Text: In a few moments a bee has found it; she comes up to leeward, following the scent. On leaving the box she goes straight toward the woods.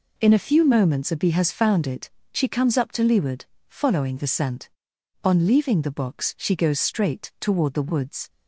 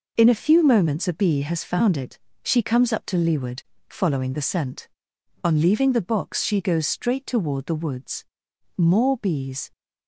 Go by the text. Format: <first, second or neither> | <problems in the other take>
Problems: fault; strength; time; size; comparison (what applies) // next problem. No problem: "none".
first | goes on to say "More bees"; noticeable; from 8.7 s on; 0.94 s long